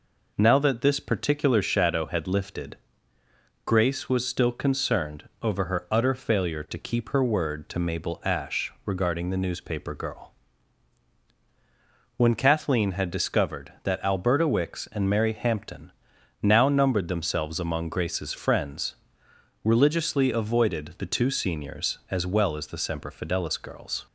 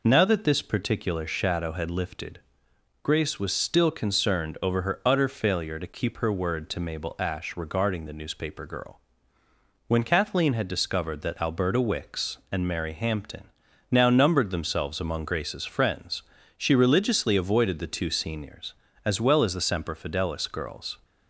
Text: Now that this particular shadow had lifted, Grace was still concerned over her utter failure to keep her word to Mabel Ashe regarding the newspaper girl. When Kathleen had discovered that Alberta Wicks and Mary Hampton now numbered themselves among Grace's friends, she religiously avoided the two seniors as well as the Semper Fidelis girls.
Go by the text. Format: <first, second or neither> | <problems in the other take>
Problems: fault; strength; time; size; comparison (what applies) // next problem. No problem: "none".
second | pauses between "Hampton" and "now"; noticeable; at 15.9 s; 0.52 s long; also in the second // skips "she"; at 19.2 s